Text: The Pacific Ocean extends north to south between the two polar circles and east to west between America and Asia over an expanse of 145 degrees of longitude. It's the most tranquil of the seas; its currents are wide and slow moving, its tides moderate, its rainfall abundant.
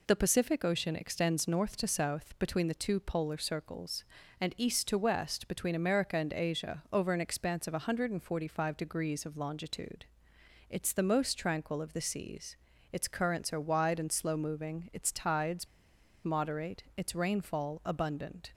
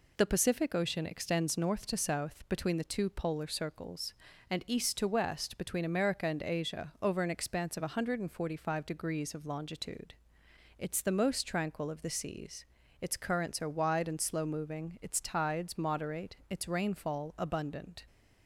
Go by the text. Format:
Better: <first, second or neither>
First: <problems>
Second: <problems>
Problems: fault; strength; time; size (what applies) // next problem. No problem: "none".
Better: second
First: pauses between "tides" and "moderate"; noticeable; at 15.6 s; 0.56 s long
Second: none